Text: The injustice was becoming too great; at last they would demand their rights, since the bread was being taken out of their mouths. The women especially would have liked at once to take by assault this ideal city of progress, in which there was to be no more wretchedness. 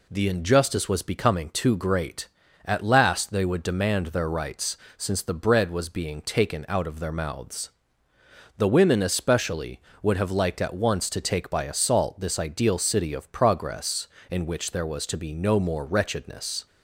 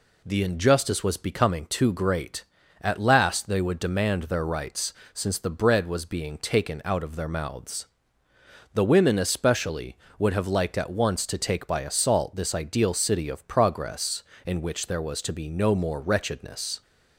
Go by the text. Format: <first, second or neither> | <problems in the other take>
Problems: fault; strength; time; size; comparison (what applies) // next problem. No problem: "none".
neither | none